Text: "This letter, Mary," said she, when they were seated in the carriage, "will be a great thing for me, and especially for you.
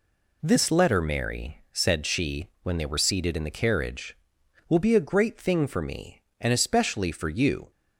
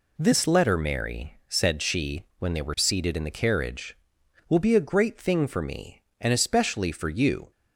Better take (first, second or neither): neither